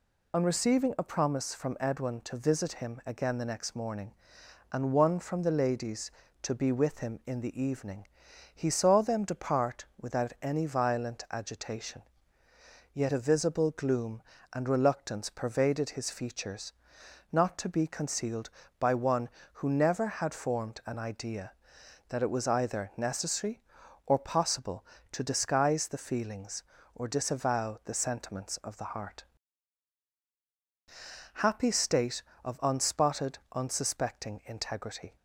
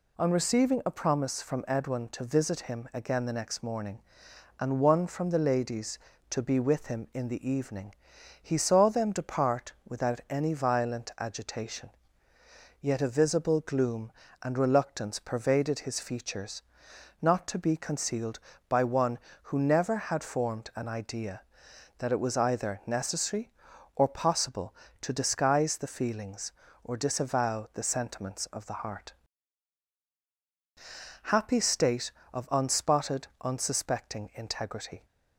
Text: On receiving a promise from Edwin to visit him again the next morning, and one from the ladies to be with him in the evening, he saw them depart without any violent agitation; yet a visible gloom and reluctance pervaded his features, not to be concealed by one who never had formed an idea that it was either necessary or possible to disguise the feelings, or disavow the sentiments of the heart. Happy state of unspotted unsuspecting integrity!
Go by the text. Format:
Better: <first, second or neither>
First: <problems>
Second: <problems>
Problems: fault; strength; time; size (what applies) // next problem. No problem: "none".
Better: second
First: loses the start of "On"; at 0.3 s; 45 ms // pauses between "depart" and "without"; slight; at 9.8 s; 0.16 s long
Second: pauses between "depart" and "without"; slight; at 9.7 s; 0.16 s long